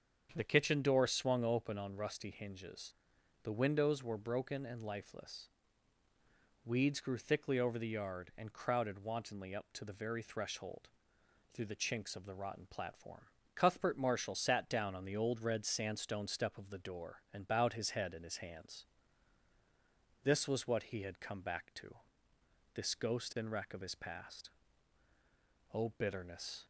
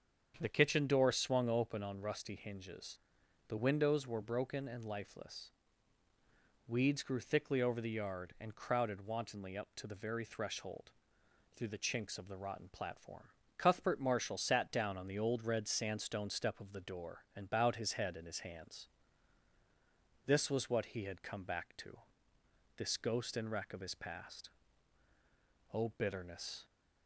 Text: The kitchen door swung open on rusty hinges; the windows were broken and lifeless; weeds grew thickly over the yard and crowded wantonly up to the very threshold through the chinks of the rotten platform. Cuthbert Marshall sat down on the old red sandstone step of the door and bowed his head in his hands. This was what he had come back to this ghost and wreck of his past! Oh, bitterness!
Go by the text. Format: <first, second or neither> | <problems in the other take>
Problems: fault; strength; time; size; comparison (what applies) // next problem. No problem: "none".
neither | starts louder than the rest; strong; the same in both // pauses between "threshold" and "through"; noticeable; the same in both // pauses between "to" and "this"; noticeable; the same in both